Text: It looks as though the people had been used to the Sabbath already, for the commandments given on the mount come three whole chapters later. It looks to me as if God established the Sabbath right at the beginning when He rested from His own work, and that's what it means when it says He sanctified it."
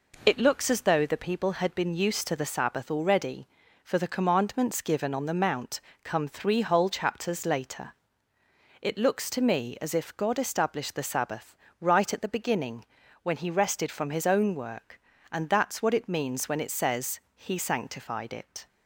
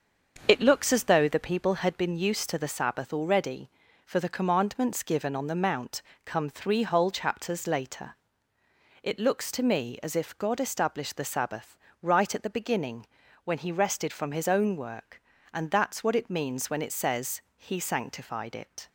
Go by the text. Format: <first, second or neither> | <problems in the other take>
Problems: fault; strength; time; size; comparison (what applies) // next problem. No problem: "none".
first | starts louder than the rest; until 2.2 s; 6.5 dB // pauses between "mount" and "come"; slight; at 6.0 s; 0.22 s long; slight in the first // pauses between "Sabbath" and "right"; slight; at 11.7 s; 0.24 s long; slight in the first // pauses between "beginning" and "when"; slight; at 13.0 s; 0.34 s long; slight in the first // pauses between "says" and "He"; slight; at 17.4 s; 0.16 s long; slight in the first